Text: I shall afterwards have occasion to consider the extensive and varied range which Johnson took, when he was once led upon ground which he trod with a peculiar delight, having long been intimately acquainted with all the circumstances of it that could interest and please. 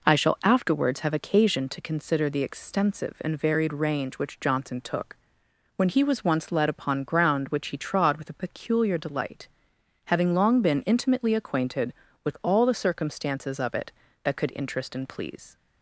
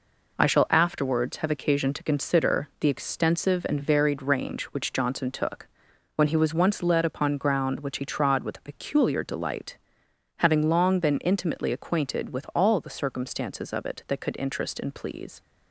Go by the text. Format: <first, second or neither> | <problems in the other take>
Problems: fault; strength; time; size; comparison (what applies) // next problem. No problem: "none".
first | gets quieter; throughout; 6.5 dB